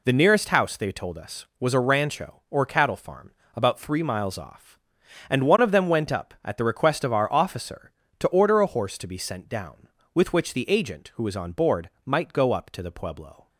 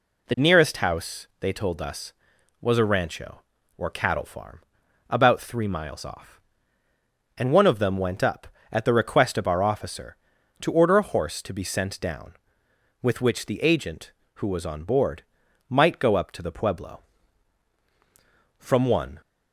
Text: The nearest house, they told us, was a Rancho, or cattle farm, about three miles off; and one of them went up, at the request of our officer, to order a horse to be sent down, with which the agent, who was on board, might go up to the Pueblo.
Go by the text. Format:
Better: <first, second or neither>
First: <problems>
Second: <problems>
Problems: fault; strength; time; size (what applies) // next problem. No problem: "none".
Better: first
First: none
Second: goes on to say "From one"; noticeable; from 18.5 s on; 0.62 s long